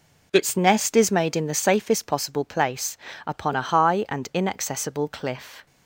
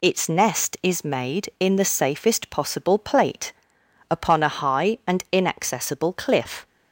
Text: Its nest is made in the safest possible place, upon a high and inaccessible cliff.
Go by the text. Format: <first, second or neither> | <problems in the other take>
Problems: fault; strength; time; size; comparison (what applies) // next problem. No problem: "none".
first | says "plate" for "place"; at 2.9 s